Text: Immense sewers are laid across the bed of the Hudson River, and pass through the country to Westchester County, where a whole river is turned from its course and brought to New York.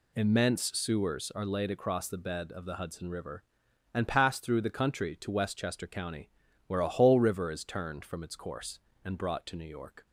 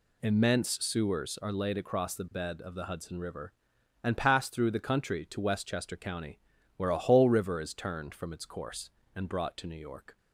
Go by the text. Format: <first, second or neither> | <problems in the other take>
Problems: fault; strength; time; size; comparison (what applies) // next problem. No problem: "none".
neither | none